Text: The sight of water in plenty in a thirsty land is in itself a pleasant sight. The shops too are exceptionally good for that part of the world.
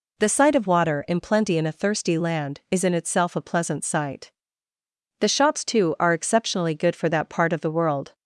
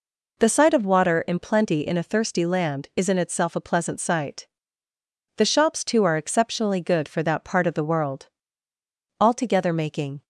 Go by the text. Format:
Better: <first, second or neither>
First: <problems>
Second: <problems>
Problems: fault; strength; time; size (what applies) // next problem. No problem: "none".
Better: first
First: none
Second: goes on to say "Altogether making"; noticeable; from 9.2 s on; 1.0 s long